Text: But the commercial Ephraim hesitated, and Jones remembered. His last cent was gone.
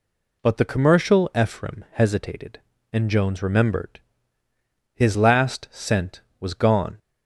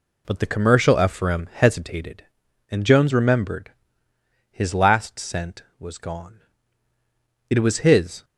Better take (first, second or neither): first